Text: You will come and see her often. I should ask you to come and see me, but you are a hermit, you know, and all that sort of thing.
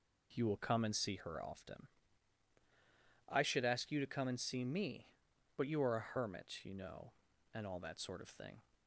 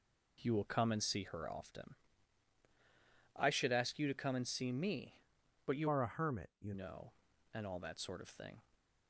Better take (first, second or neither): first